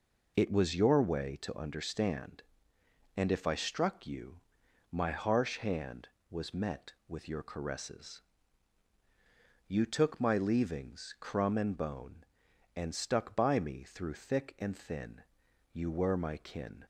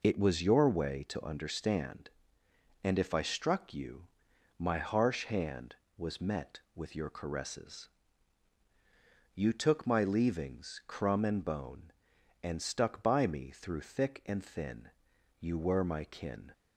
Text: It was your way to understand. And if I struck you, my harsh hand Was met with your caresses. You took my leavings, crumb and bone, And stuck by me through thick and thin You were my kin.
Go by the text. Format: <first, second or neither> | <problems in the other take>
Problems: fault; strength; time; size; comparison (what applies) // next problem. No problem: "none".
neither | pauses between "thin" and "You"; noticeable; the same in both